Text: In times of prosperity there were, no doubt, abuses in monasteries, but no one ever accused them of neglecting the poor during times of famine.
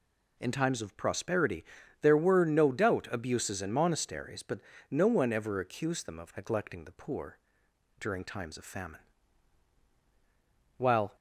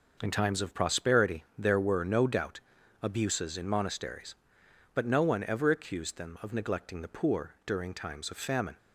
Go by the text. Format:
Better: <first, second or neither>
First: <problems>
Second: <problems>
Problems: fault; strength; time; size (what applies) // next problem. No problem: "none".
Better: second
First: pauses between "prosperity" and "there"; at 1.6 s; 0.38 s long // pauses between "but" and "no"; slight; at 4.5 s; 0.32 s long // pauses between "poor" and "during"; noticeable; at 7.3 s; 0.62 s long // goes on to say "While"; slight; from 10.7 s on; 0.38 s long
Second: pauses between "prosperity" and "there"; slight; at 1.4 s; 0.16 s long